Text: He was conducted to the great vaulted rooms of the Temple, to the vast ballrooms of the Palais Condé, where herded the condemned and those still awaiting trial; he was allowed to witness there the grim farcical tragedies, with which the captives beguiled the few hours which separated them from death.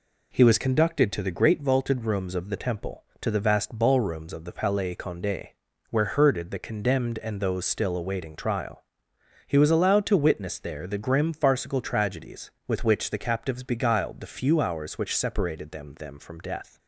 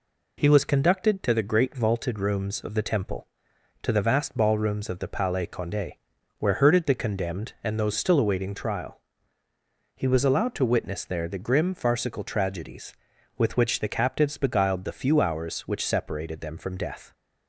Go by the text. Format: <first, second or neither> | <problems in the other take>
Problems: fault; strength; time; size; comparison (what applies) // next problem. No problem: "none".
second | says "them" twice; at 15.9 s